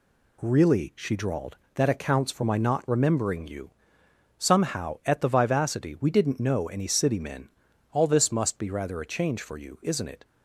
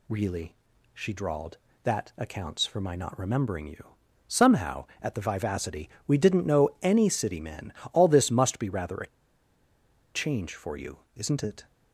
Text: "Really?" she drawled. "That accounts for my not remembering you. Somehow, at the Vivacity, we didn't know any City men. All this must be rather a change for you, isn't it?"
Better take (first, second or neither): first